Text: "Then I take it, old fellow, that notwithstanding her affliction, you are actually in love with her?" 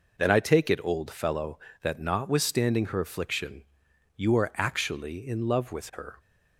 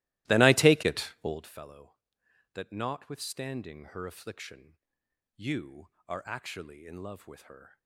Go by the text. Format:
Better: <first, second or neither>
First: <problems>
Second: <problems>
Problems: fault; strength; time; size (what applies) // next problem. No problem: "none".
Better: first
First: none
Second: starts louder than the rest; strong; until 1.4 s; 17.5 dB